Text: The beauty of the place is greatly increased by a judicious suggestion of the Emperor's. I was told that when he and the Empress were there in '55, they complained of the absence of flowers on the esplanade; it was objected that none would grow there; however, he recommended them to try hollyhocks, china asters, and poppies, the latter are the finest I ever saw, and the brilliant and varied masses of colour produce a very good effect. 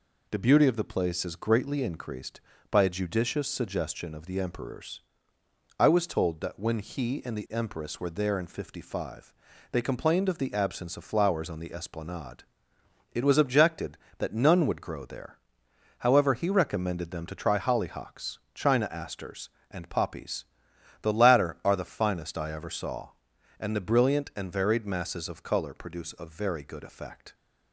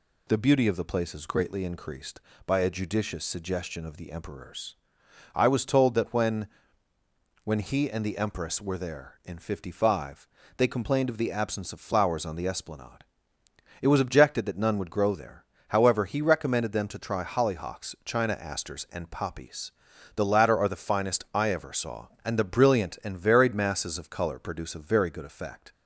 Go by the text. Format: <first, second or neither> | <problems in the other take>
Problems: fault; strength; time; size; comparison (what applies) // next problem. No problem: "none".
first | says "when" twice; at 7.4 s